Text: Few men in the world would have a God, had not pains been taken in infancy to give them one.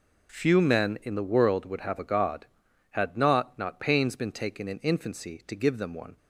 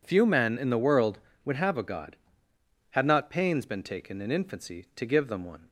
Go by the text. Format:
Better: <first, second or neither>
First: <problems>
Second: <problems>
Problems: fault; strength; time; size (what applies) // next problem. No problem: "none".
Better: second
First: says "not" twice; at 3.5 s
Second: none